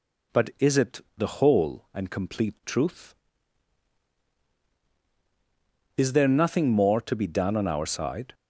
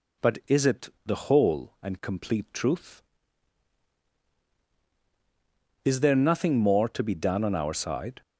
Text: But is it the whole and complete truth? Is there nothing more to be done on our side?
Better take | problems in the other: neither | pauses between "it" and "the"; slight; the same in both

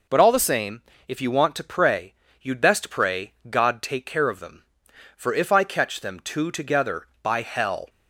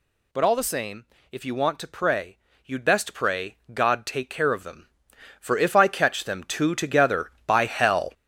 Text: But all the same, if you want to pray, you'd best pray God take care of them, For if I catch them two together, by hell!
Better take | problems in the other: first | gets louder; strong; throughout; 7.5 dB // pauses between "pray" and "God"; slight; at 3.5 s; 0.16 s long; slight in the first

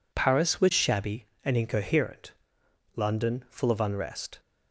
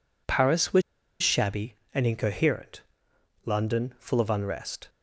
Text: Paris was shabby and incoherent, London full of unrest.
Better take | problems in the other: first | pauses between "was" and "shabby"; at 0.8 s; 0.41 s long

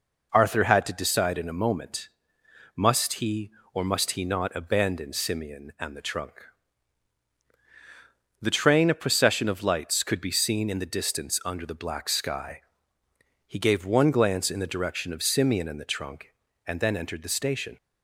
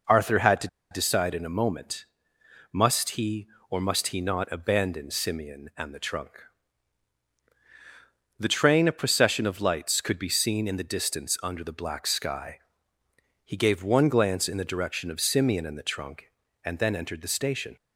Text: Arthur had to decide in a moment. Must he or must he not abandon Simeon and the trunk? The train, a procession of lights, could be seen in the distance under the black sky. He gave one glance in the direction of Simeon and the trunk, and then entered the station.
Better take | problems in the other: first | pauses between "to" and "decide"; slight; at 0.6 s; 0.22 s long

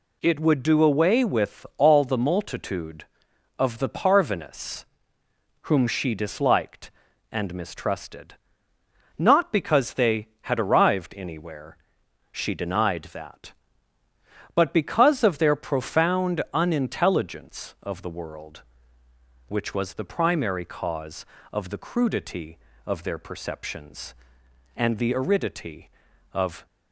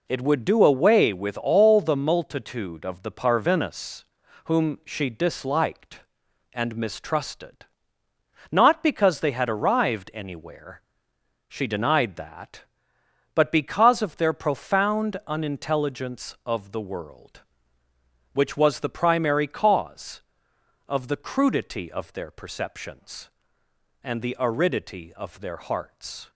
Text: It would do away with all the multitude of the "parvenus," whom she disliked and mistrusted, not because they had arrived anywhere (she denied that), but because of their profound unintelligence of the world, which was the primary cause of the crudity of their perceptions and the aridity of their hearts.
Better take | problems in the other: second | stops before "their hearts"; at 26.6 s

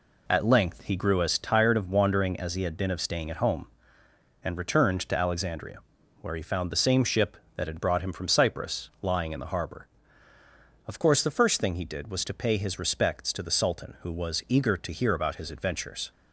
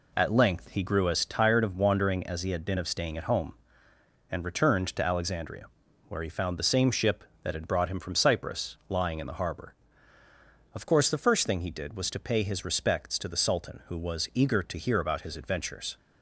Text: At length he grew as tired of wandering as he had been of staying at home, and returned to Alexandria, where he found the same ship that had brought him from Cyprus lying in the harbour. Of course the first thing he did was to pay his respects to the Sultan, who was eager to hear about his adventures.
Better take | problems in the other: neither | none

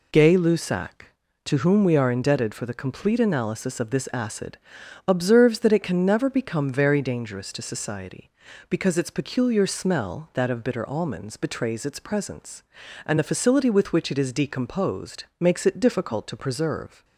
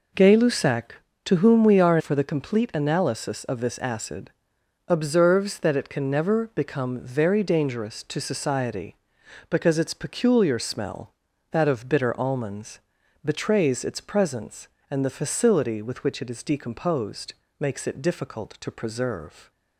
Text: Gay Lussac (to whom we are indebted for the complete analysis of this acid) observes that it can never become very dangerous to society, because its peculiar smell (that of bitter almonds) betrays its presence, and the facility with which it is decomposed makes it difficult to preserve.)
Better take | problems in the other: first | skips "indebted"; at 1.9 s // pauses between "decomposed" and "makes"; slight; at 17.3 s; 0.24 s long; slight in the first

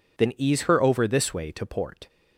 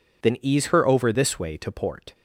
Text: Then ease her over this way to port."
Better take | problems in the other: neither | none

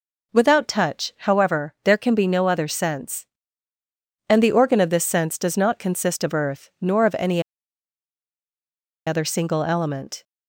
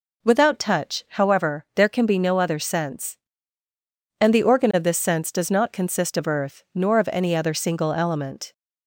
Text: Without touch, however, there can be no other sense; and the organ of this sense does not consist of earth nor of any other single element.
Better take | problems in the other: second | pauses between "any" and "other"; strong; at 7.4 s; 1.6 s long

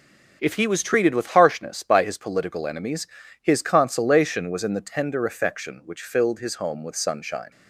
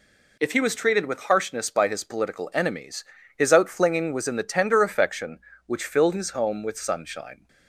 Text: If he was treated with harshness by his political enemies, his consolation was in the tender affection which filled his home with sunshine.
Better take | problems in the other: first | says "outflinging" for "consolation"; at 3.5 s

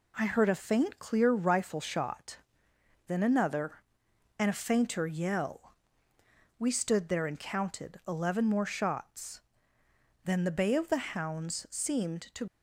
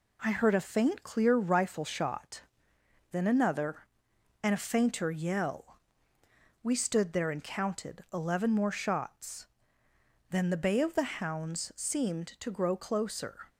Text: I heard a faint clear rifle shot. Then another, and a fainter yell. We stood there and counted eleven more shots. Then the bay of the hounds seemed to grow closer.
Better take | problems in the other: second | stops before "grow closer"; at 12.4 s

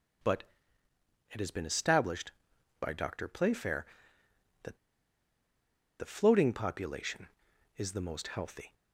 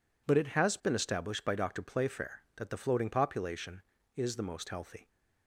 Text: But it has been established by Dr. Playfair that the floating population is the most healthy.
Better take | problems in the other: second | pauses between "But" and "it"; noticeable; at 0.4 s; 0.88 s long // pauses between "that" and "the"; at 4.7 s; 1.2 s long

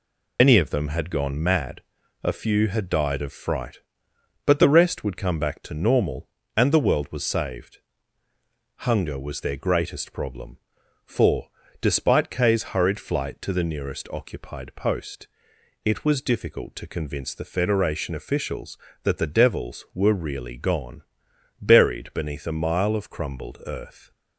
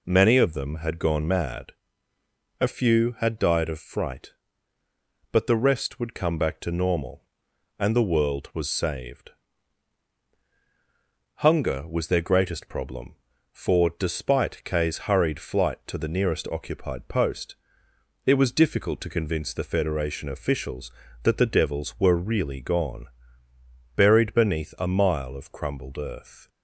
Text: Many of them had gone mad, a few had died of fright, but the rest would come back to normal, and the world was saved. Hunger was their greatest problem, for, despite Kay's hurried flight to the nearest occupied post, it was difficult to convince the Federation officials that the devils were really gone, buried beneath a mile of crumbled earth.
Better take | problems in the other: second | loses the start of "Many"; at 0.3 s; 90 ms

